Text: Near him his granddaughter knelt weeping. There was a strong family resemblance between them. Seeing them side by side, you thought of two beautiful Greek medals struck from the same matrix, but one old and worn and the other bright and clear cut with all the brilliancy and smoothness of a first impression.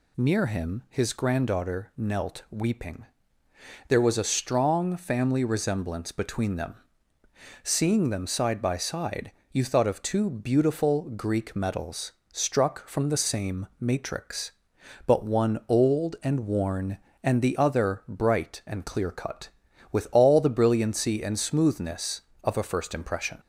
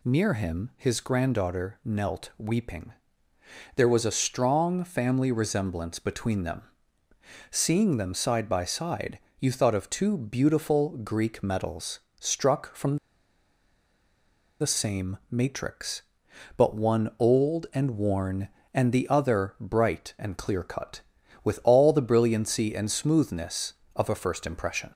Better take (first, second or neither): first